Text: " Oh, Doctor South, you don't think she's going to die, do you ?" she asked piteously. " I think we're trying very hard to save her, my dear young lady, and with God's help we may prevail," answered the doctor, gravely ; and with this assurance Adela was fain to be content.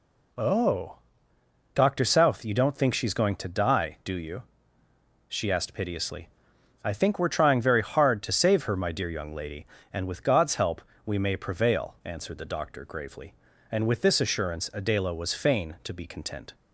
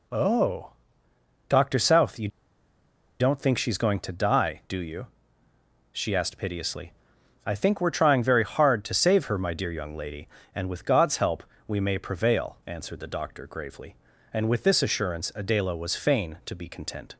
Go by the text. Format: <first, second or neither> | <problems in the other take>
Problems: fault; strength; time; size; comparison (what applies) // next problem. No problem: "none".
first | pauses between "you" and "don't"; noticeable; at 2.2 s; 0.91 s long // pauses between "help" and "we"; slight; at 11.4 s; 0.24 s long; slight in the first